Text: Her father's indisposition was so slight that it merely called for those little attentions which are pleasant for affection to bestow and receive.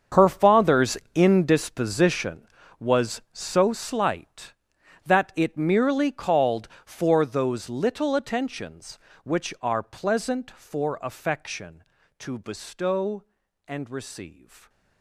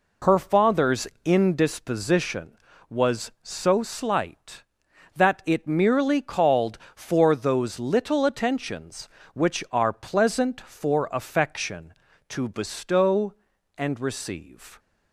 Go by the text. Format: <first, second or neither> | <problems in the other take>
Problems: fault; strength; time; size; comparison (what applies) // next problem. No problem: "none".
second | gets quieter; strong; throughout; 15.5 dB // pauses between "father's" and "indisposition"; slight; at 0.9 s; 0.20 s long; slight in the second